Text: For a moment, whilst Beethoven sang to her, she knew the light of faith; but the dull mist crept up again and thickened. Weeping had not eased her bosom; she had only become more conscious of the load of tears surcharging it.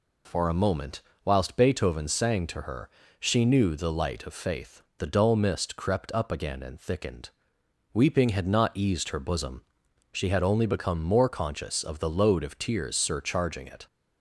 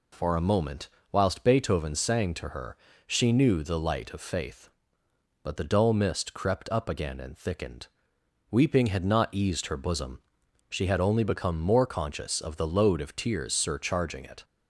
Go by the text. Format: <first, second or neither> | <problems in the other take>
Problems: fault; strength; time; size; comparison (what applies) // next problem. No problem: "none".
second | skips "but"; at 4.9 s